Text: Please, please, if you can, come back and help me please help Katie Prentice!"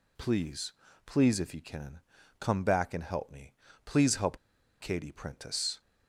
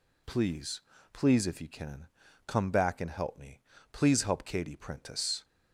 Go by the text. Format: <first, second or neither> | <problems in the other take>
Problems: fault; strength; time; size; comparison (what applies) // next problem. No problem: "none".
second | pauses between "me" and "please"; slight; at 3.5 s; 0.32 s long; slight in the second // pauses between "help" and "Katie"; at 4.3 s; 0.43 s long